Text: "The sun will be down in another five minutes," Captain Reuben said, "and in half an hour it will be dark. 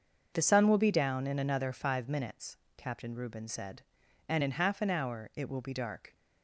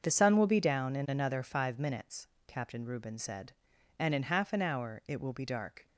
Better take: neither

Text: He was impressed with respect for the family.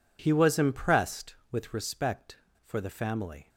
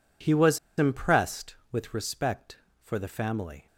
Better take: first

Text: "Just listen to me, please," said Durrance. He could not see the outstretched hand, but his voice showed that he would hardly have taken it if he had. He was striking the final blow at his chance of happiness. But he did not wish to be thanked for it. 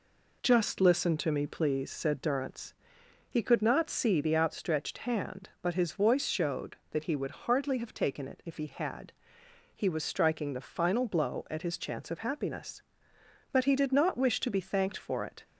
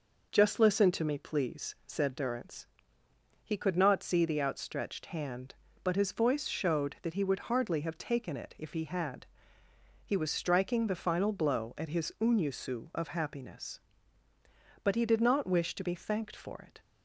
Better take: first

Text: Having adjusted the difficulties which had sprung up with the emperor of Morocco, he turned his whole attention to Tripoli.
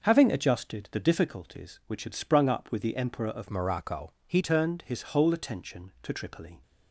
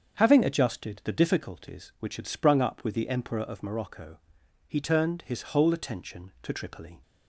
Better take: second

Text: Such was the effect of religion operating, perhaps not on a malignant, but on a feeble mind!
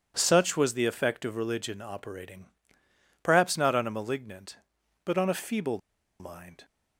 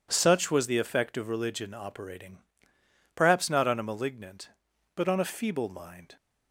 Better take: second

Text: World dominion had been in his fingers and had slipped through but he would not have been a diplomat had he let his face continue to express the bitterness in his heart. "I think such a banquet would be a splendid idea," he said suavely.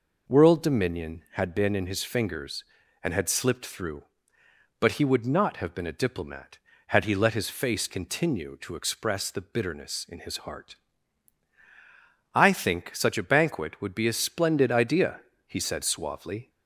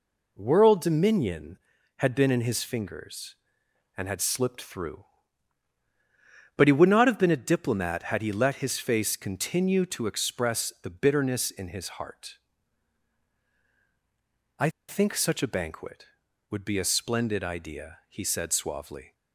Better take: first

